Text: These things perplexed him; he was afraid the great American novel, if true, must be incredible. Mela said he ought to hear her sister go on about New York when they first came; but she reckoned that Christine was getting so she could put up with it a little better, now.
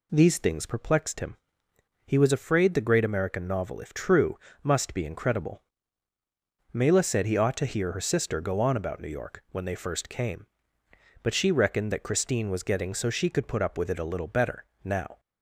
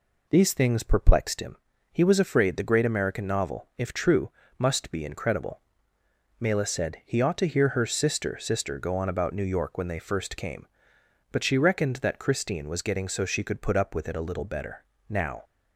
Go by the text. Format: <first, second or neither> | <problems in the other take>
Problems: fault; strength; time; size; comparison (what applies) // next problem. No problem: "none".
first | says "sister" twice; at 8.3 s